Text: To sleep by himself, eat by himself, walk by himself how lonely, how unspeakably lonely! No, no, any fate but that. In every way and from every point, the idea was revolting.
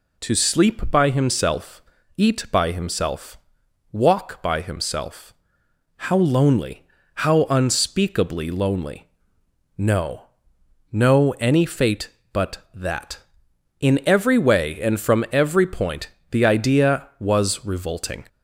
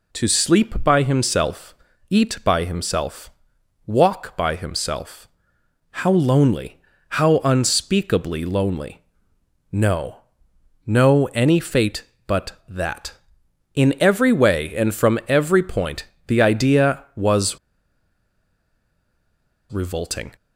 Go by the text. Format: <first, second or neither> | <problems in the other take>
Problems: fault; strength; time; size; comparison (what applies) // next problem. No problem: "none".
first | pauses between "himself" and "how"; noticeable; at 5.2 s; 0.62 s long; noticeable in the first // pauses between "was" and "revolting"; strong; at 17.5 s; 2.1 s long